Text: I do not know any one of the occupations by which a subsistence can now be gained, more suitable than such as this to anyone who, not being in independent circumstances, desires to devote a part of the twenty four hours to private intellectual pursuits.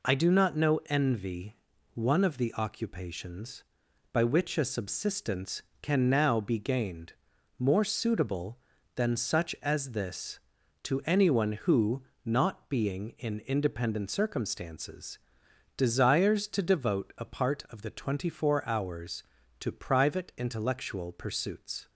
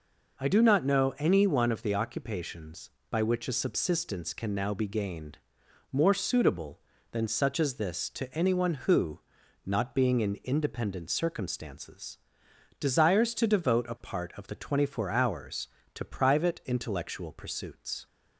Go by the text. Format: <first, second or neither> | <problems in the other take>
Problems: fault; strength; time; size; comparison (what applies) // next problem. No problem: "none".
second | says "envy" for "any"; at 0.8 s